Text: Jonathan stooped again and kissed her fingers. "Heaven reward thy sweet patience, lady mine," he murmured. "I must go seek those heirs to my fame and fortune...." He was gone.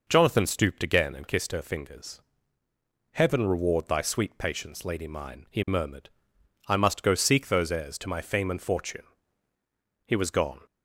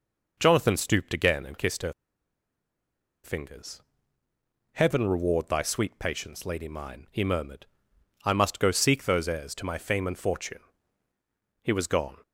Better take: first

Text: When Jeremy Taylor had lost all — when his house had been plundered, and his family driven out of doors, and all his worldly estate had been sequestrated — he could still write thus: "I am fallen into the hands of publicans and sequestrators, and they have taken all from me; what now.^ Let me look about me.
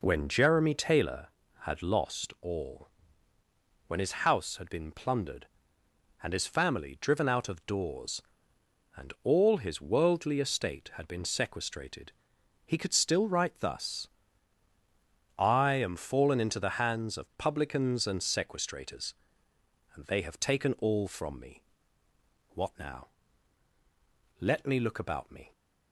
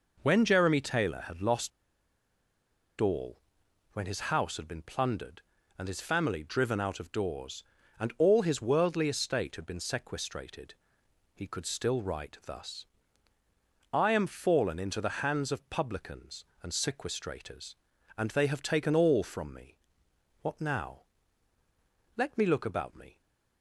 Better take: first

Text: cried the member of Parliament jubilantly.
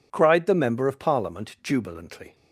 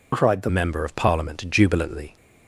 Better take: first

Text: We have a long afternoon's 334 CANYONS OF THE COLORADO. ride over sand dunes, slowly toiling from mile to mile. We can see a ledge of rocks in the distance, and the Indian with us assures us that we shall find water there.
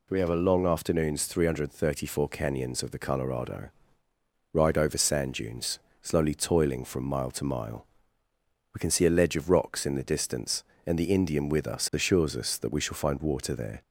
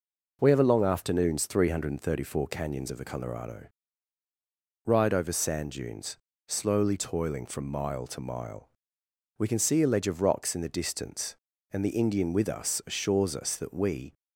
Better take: first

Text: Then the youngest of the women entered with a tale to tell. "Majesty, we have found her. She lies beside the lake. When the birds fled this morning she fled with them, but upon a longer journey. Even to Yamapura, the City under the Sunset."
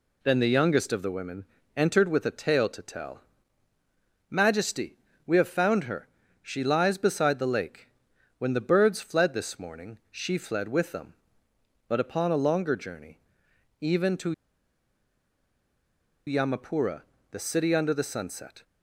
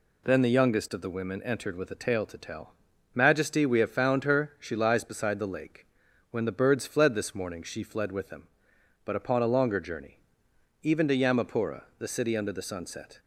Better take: second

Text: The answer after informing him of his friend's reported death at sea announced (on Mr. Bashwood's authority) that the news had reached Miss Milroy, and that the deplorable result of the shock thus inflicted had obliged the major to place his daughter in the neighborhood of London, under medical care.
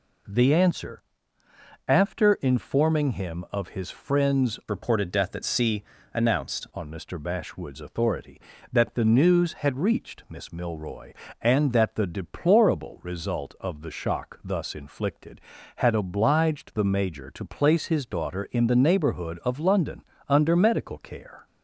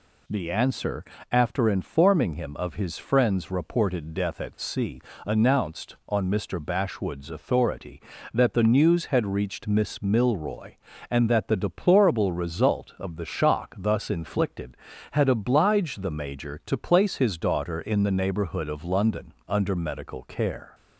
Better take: second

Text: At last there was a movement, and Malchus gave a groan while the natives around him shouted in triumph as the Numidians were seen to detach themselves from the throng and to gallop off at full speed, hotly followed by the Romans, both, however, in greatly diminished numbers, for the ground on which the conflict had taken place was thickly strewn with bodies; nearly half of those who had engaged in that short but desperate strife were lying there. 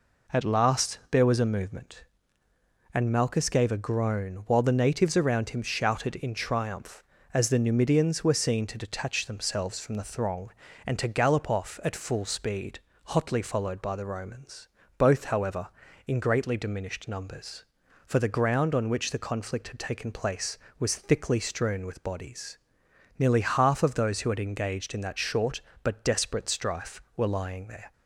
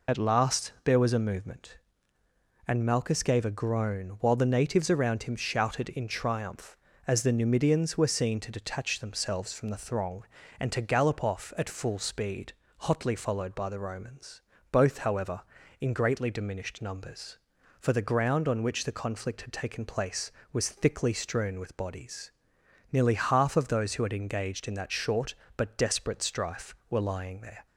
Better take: first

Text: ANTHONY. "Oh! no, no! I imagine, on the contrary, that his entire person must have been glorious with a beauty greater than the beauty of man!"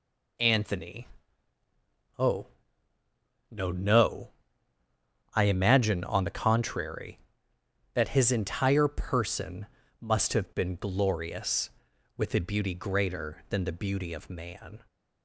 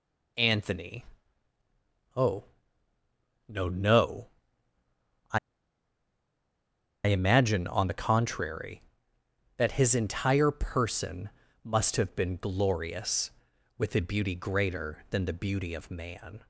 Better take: first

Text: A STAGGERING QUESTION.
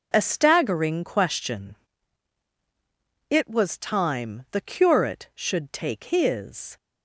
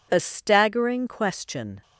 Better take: second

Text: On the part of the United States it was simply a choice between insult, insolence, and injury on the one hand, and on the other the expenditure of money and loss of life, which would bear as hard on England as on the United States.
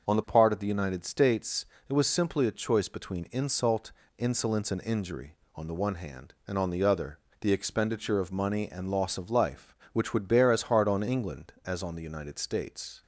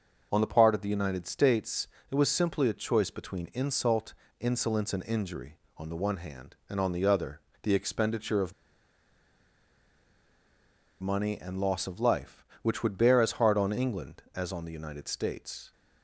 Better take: first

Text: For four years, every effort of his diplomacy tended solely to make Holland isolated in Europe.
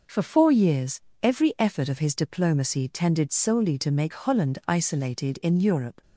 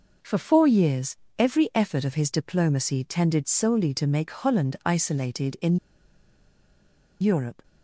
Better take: first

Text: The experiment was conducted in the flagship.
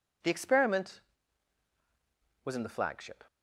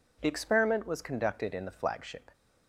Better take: second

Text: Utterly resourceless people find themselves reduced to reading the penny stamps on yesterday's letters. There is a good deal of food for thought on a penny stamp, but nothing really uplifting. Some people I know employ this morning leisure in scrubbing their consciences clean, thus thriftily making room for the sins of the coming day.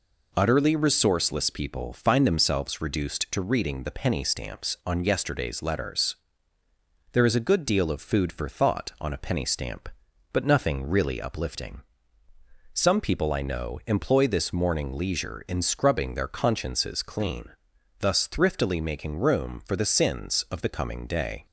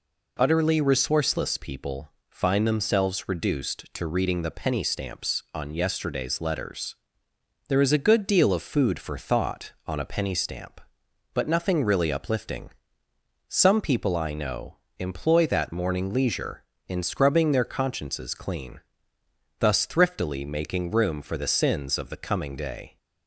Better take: first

